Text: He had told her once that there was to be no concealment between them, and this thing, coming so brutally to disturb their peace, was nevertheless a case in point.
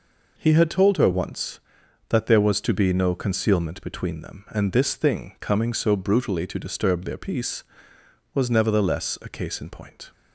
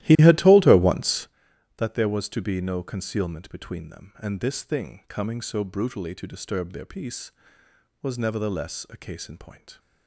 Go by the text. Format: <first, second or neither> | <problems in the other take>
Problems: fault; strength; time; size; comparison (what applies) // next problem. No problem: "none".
first | starts louder than the rest; strong; until 1.3 s; 15 dB